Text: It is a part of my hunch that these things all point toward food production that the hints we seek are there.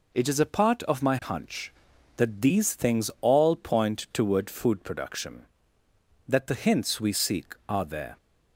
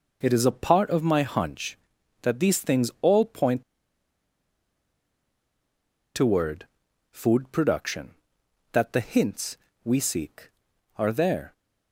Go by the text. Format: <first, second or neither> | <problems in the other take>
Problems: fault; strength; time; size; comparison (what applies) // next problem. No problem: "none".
first | pauses between "point" and "toward"; strong; at 3.6 s; 2.5 s long // pauses between "toward" and "food"; noticeable; at 6.6 s; 0.46 s long // pauses between "hints" and "we"; slight; at 9.5 s; 0.26 s long